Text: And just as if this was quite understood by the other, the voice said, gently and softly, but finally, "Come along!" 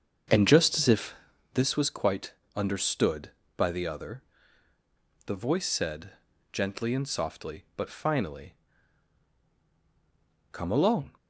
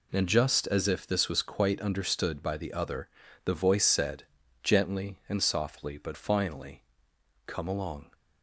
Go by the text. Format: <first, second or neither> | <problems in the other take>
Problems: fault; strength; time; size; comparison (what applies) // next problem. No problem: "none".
second | starts louder than the rest; until 1.3 s; 7 dB // pauses between "if" and "this"; at 1.1 s; 0.40 s long // pauses between "quite" and "understood"; slight; at 2.3 s; 0.22 s long